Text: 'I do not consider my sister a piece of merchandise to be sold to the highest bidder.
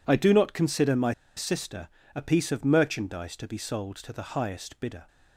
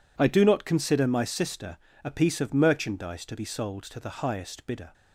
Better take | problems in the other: second | pauses between "my" and "sister"; slight; at 1.1 s; 0.23 s long // pauses between "sister" and "a"; slight; at 1.8 s; 0.26 s long; slight in the second

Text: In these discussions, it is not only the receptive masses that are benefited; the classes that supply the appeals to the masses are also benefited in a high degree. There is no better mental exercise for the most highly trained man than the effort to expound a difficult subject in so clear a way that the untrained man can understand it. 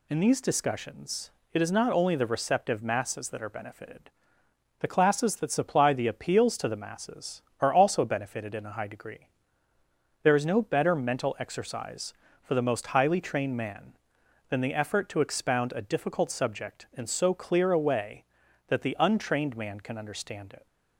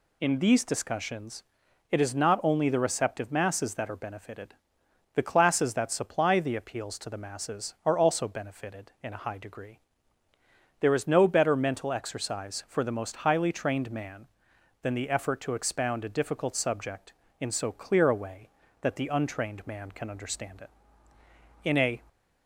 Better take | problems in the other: first | goes on to say "In a"; slight; from 21.6 s on; 0.36 s long

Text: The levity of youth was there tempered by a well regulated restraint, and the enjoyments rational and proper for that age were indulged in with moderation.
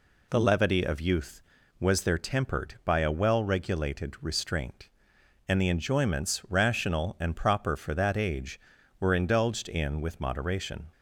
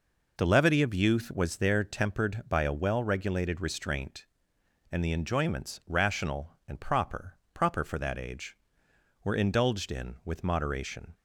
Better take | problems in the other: first | says "proper" twice; at 7.5 s

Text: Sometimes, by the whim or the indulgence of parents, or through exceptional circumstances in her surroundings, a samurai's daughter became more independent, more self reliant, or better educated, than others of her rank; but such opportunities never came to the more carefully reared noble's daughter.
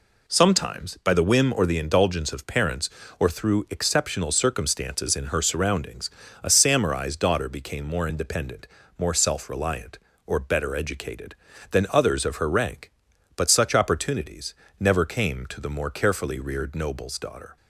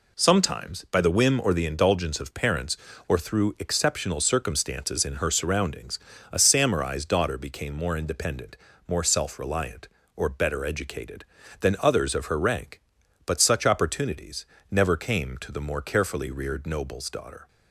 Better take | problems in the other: neither | pauses between "opportunities" and "never"; slight; the same in both

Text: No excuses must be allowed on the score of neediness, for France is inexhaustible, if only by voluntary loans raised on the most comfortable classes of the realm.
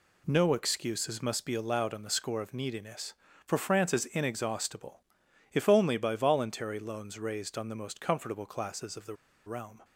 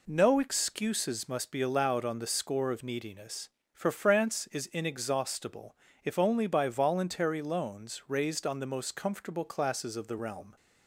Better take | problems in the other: second | pauses between "the" and "realm"; slight; at 9.1 s; 0.31 s long

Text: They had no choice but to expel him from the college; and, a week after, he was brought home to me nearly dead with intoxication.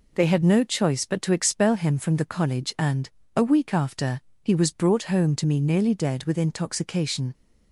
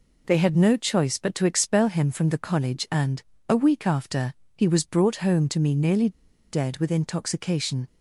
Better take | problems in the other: first | pauses between "nearly" and "dead"; at 6.0 s; 0.41 s long

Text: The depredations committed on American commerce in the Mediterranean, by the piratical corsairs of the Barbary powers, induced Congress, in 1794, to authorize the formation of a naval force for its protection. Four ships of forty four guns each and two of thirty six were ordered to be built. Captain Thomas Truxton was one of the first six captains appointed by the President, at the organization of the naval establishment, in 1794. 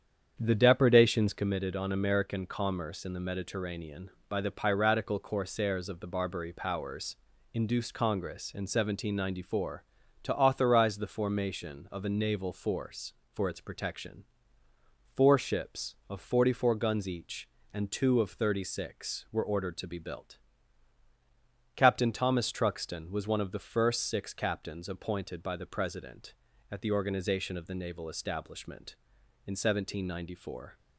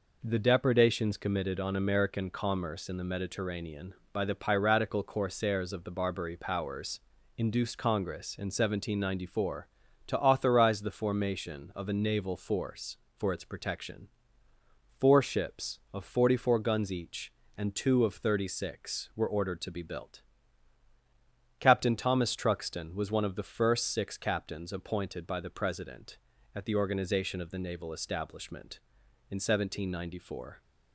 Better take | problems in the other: second | starts louder than the rest; strong; until 1.5 s; 8 dB

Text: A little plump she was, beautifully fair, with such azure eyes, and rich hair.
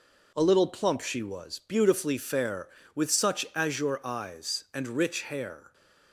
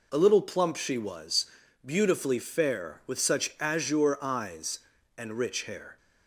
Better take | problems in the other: neither | none

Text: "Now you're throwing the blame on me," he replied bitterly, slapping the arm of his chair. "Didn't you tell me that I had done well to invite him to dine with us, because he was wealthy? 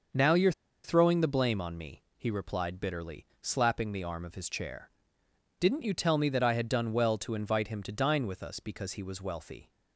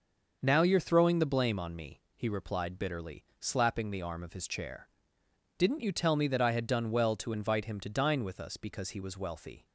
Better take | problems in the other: second | starts louder than the rest; until 1.4 s; 6 dB; noticeable in the second // pauses between "you're" and "throwing"; slight; at 0.5 s; 0.33 s long

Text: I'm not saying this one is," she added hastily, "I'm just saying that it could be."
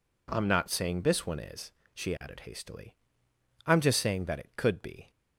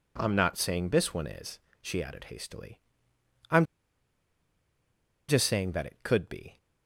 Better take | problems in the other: first | pauses between "I'm" and "just"; strong; at 3.6 s; 1.6 s long

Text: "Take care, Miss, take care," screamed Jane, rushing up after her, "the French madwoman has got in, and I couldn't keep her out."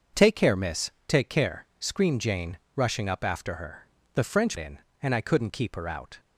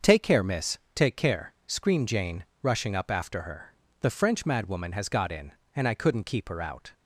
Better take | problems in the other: second | starts louder than the rest; until 1.3 s; 6.5 dB; also in the second // skips "madwoman has got"; at 4.5 s

